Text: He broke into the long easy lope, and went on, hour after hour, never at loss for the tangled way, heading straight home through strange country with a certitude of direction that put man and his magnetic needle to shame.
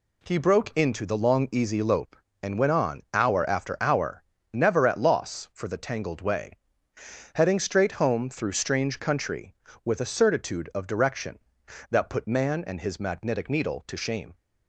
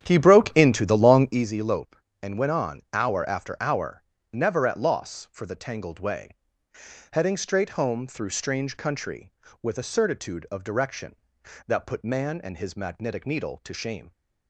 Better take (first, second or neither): first